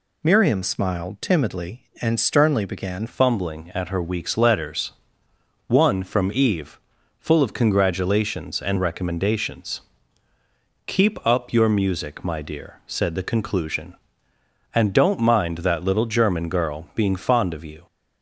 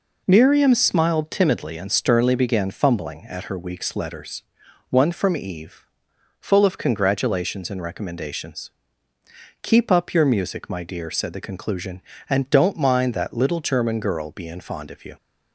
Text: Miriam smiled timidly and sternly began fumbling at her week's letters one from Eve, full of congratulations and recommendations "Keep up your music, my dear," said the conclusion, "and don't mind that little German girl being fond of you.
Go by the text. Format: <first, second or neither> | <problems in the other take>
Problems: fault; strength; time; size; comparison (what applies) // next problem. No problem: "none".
second | changes voice at "fumbling"; from 3.0 s on; 14.8 s long // pauses between "letters" and "one"; noticeable; at 4.9 s; 0.76 s long; noticeable in the second // pauses between "recommendations" and "Keep"; at 9.8 s; 1.0 s long; noticeable in the second